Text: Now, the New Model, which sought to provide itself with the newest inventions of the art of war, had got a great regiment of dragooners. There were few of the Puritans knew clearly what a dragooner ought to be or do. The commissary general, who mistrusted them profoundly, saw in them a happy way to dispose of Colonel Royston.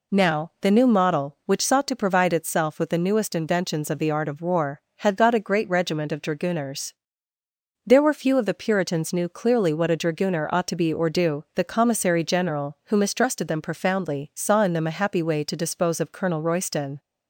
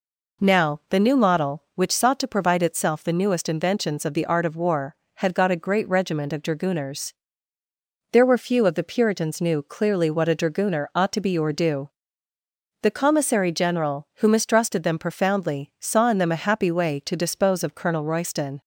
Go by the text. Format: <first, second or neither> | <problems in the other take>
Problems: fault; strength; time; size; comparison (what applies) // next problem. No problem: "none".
first | skips "with"; at 3.0 s